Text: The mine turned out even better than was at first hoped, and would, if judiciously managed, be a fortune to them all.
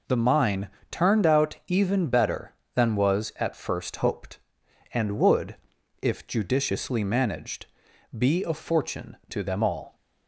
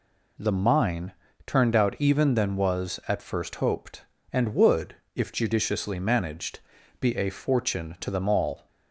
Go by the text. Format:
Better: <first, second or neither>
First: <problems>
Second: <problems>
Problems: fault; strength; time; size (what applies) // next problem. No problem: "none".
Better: first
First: pauses between "mine" and "turned"; slight; at 0.6 s; 0.22 s long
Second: pauses between "mine" and "turned"; slight; at 1.1 s; 0.32 s long // skips "better"; at 2.3 s